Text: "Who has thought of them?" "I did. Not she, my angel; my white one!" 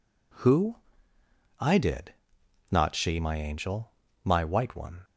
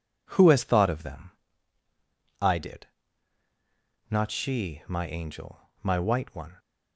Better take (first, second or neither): second